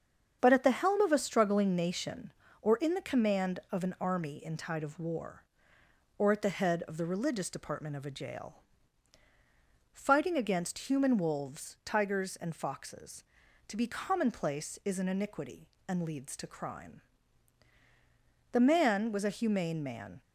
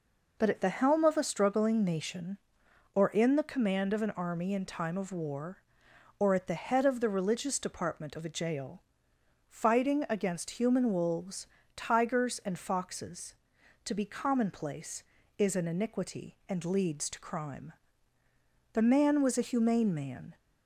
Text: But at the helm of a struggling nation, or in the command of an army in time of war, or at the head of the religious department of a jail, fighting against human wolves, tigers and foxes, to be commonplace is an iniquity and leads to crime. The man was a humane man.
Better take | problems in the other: second | starts louder than the rest; strong; until 1.4 s; 7.5 dB // says "tide" for "time"; at 4.5 s

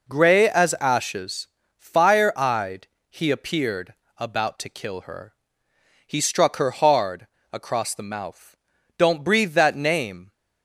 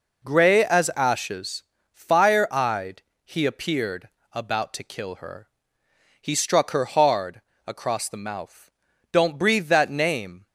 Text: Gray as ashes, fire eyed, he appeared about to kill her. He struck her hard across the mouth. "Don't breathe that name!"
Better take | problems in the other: neither | pauses between "appeared" and "about"; slight; the same in both // pauses between "hard" and "across"; slight; the same in both

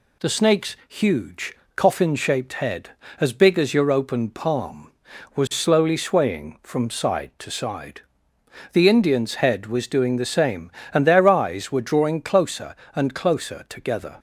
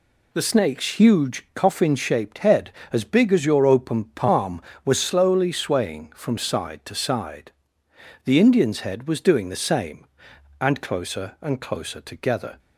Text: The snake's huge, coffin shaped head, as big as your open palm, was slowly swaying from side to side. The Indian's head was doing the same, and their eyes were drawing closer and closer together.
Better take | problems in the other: first | skips "their eyes were drawing"; at 10.8 s

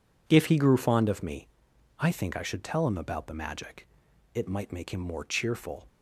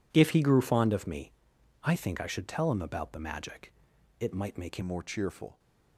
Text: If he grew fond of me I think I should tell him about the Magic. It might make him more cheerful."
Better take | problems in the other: first | pauses between "me" and "I"; noticeable; at 1.3 s; 0.54 s long; noticeable in the first // changes voice at "more"; from 4.8 s on; 0.7 s long

